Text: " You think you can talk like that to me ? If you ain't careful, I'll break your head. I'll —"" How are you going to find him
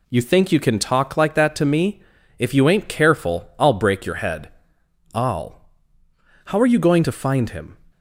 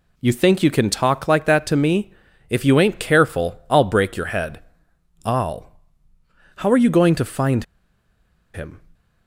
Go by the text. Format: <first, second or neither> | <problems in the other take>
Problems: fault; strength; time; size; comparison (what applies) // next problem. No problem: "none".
first | pauses between "find" and "him"; noticeable; at 7.6 s; 0.89 s long